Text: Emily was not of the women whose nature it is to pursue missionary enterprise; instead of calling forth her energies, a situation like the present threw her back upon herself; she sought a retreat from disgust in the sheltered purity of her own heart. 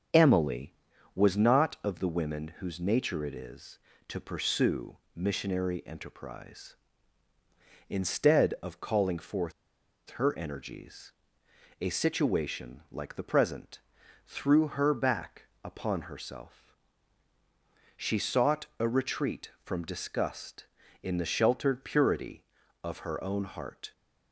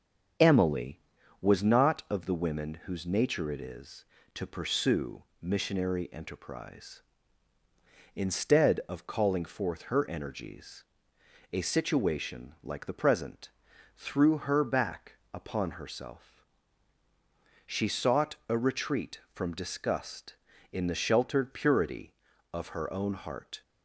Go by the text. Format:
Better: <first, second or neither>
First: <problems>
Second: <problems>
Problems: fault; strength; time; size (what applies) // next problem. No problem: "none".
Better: second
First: starts louder than the rest; until 1.5 s; 7 dB // pauses between "pursue" and "missionary"; slight; at 4.9 s; 0.18 s long // pauses between "forth" and "her"; noticeable; at 9.5 s; 0.65 s long // pauses between "present" and "threw"; noticeable; at 13.7 s; 0.48 s long // pauses between "back" and "upon"; slight; at 15.4 s; 0.18 s long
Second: starts louder than the rest; until 1.8 s; 7 dB // pauses between "pursue" and "missionary"; slight; at 5.2 s; 0.18 s long // pauses between "present" and "threw"; noticeable; at 13.4 s; 0.48 s long // pauses between "back" and "upon"; slight; at 15.1 s; 0.17 s long